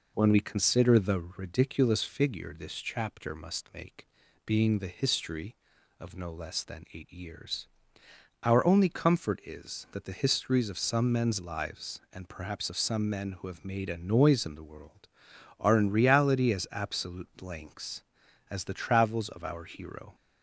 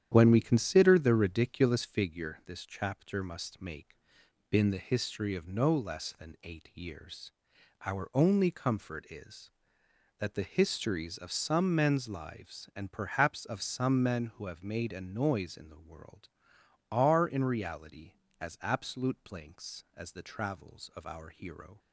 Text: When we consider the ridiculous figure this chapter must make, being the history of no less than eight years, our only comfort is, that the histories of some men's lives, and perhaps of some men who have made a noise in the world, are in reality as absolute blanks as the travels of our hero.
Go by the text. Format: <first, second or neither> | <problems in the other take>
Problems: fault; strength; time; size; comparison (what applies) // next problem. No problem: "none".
first | starts louder than the rest; strong; until 1.1 s; 10 dB // says "been" for "being"; at 4.5 s